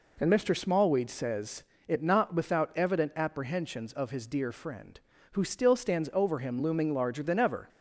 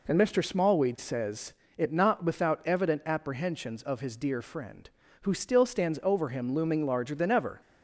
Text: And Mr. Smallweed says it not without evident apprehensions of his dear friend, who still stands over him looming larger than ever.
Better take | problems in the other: neither | pauses between "says" and "it"; slight; the same in both

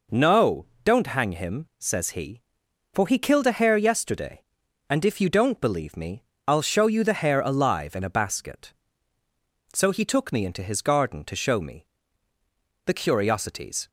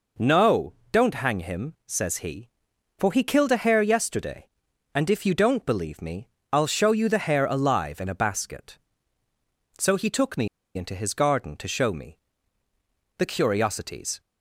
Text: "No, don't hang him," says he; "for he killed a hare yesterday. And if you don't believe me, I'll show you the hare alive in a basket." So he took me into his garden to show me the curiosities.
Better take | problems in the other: first | pauses between "me" and "into"; slight; at 10.4 s; 0.28 s long // pauses between "me" and "the"; noticeable; at 12.1 s; 0.98 s long; noticeable in the first

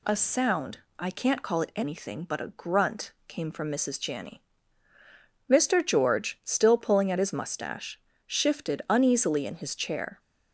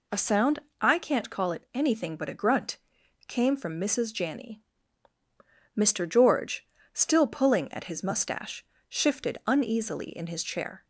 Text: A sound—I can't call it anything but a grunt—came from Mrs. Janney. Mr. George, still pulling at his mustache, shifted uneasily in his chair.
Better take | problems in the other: neither | none

